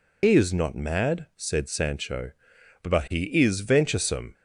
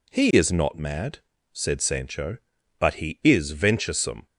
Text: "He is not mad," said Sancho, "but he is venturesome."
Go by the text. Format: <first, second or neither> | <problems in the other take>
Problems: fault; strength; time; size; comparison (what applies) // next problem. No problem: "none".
second | loses the start of "He"; at 0.2 s; 60 ms